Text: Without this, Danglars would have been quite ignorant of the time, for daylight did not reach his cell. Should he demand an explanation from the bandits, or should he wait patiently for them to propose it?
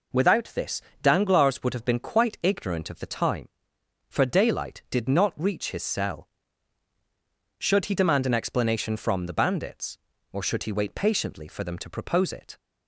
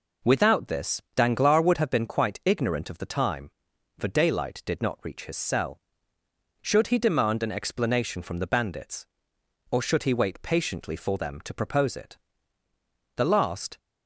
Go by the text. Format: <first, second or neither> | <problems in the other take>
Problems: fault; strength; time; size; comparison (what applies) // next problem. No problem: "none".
first | goes on to say "The last"; from 13.1 s on; 0.60 s long